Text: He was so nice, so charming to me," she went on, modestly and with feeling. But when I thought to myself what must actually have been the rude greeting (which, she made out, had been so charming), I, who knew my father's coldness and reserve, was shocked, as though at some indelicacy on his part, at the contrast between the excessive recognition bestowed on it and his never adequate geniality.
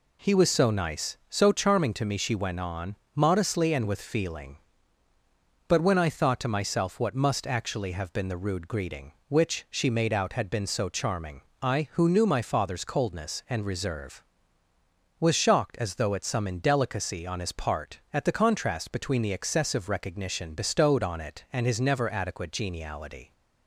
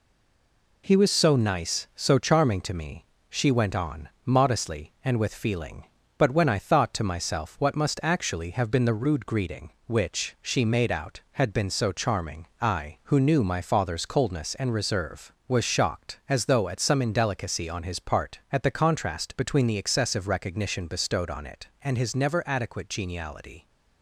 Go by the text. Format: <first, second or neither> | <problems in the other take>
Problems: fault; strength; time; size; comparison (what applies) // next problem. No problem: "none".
first | stays silent before the first word; slight; until 0.8 s; 0.8 s long